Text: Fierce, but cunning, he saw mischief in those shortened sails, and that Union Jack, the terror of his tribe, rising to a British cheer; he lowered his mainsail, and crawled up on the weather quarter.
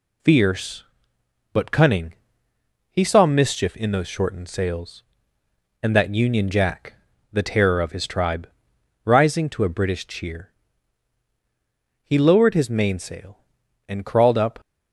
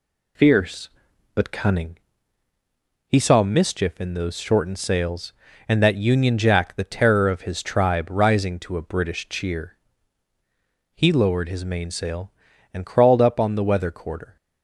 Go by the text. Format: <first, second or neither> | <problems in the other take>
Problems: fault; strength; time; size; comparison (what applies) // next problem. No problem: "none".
second | stops before "on the weather quarter"; at 14.5 s